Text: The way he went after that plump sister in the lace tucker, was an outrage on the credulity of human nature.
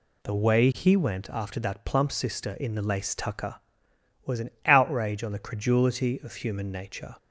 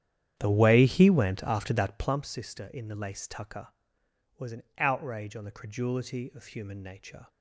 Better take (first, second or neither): first